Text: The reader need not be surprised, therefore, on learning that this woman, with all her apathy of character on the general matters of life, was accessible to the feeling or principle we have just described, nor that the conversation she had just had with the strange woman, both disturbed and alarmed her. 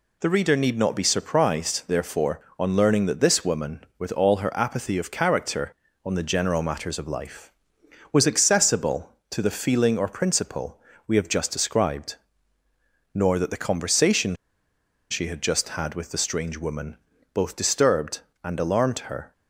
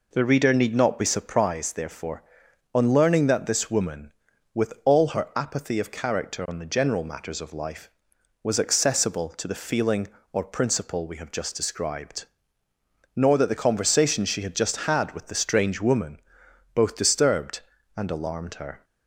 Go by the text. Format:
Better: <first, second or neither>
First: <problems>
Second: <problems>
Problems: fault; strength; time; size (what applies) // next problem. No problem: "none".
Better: second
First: pauses between "principle" and "we"; slight; at 10.7 s; 0.26 s long // pauses between "conversation" and "she"; noticeable; at 14.3 s; 0.74 s long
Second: none